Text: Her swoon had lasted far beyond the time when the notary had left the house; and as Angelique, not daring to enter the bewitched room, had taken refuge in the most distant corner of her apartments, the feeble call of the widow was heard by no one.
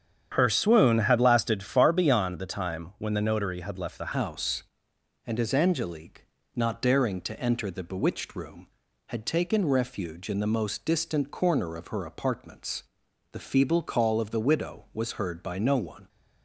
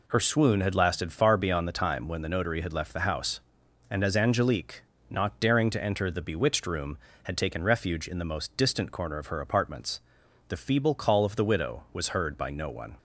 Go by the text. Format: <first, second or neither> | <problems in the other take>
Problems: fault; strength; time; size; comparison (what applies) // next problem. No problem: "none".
second | starts louder than the rest; strong; until 1.3 s; 8.5 dB // changes voice at "house"; from 4.1 s on; 11.9 s long